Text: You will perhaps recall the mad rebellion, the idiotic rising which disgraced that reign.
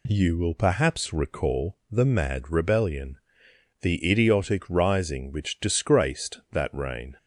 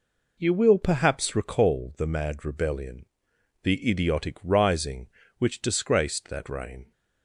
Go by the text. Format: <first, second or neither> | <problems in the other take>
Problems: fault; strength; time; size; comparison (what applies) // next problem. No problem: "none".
neither | none